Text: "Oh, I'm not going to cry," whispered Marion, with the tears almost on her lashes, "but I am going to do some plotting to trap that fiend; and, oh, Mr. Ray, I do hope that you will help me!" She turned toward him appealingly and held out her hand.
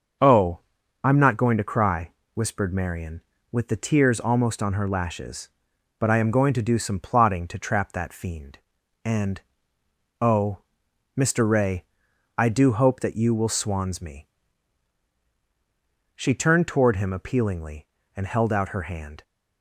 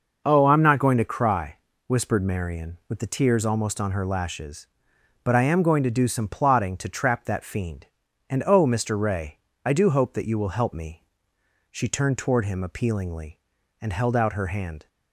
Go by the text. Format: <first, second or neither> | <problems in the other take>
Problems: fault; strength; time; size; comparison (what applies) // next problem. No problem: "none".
second | starts louder than the rest; until 1.6 s; 6.5 dB // says "swans" for "help"; at 13.5 s